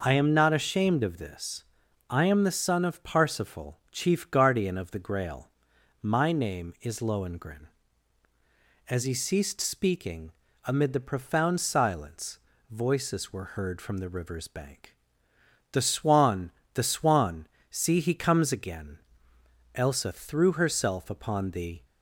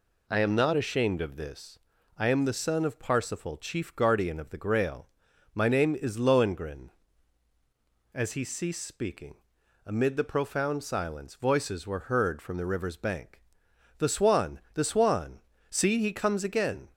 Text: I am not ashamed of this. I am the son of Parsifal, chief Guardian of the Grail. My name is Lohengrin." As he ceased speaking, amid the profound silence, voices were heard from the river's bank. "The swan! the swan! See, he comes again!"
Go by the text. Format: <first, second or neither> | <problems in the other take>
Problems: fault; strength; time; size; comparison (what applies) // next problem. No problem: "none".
second | goes on to say "Elsa threw herself upon the"; strong; from 19.7 s on; 2.0 s long